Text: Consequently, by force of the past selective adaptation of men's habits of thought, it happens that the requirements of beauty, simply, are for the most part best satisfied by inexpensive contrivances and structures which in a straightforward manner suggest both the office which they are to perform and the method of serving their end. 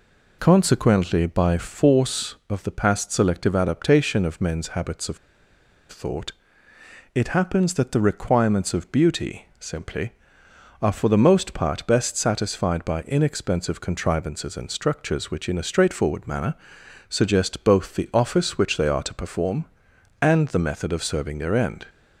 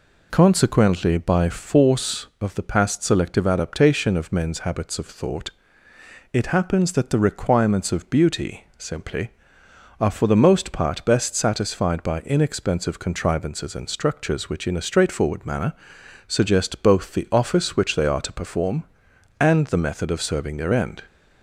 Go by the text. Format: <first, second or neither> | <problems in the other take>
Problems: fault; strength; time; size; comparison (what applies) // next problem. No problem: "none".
second | pauses between "of" and "thought"; noticeable; at 5.1 s; 0.71 s long // pauses between "manner" and "suggest"; noticeable; at 16.5 s; 0.54 s long; noticeable in the second